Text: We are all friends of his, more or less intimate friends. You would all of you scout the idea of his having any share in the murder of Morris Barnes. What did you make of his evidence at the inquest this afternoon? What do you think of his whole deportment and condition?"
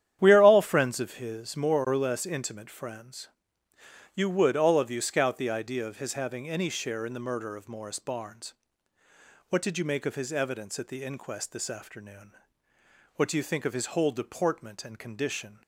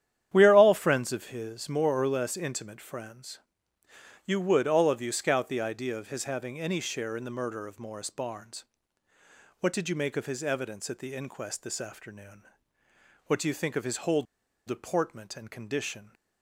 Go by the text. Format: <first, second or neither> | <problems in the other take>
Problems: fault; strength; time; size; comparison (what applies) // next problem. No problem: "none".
first | starts louder than the rest; strong; until 1.3 s; 10 dB; strong in the first // pauses between "whole" and "deportment"; at 14.2 s; 0.44 s long